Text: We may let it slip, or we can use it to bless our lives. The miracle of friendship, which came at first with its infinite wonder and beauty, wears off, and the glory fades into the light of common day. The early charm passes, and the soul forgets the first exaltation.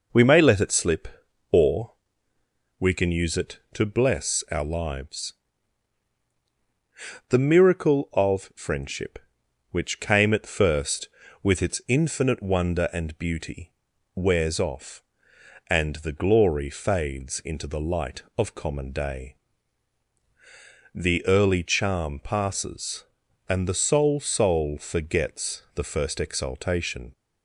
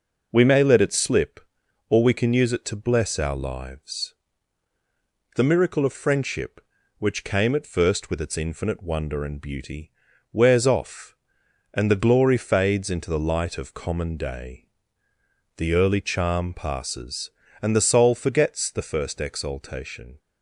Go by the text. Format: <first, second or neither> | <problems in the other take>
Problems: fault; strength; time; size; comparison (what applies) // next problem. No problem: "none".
second | pauses between "or" and "we"; noticeable; at 1.9 s; 0.88 s long // says "soul" twice; at 24.1 s